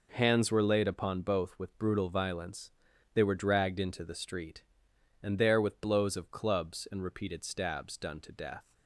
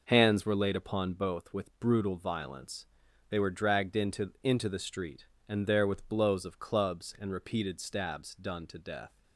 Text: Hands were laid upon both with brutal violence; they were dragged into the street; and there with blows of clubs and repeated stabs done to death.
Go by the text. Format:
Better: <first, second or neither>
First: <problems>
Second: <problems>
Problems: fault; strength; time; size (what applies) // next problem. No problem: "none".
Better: first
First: none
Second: says "into" twice; at 4.4 s